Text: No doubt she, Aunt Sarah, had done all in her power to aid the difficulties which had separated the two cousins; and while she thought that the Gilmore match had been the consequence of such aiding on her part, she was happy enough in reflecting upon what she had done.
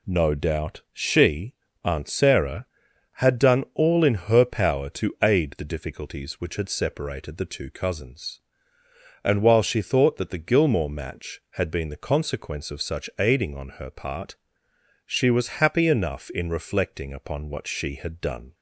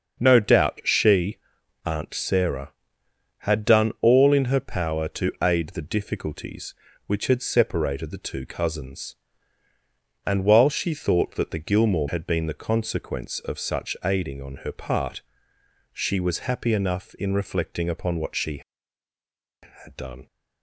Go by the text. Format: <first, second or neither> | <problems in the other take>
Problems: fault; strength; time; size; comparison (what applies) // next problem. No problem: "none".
first | starts louder than the rest; until 1.2 s; 6.5 dB // skips "match"; at 12.0 s